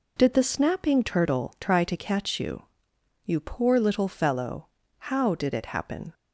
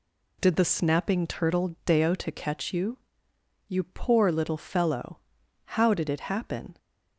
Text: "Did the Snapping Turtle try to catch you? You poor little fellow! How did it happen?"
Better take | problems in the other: first | says "deo" for "try"; at 1.8 s

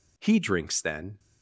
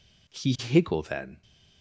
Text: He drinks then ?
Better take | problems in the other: first | says "higgle" for "drinks"; at 0.5 s

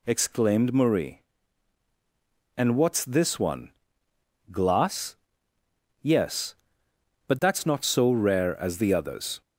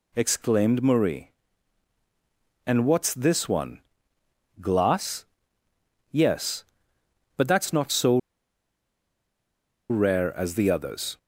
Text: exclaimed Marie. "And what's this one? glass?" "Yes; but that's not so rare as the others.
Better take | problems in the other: first | pauses between "so" and "rare"; strong; at 8.1 s; 1.7 s long

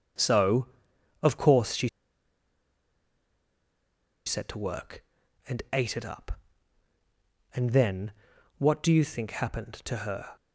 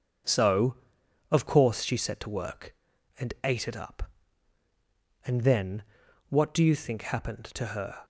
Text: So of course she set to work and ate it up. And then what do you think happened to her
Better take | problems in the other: second | pauses between "she" and "set"; strong; at 1.8 s; 2.3 s long // pauses between "then" and "what"; noticeable; at 8.1 s; 0.46 s long; noticeable in the second

